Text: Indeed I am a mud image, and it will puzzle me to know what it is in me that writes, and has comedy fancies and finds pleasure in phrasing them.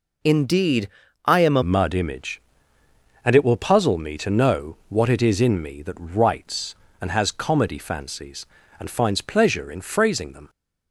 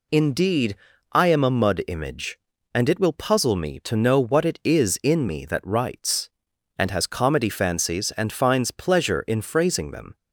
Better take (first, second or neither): second